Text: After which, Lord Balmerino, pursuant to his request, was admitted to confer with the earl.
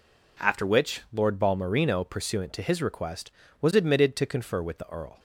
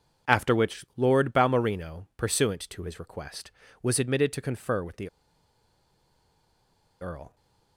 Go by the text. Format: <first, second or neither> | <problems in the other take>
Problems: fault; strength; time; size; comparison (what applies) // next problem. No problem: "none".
first | pauses between "the" and "earl"; strong; at 5.0 s; 1.9 s long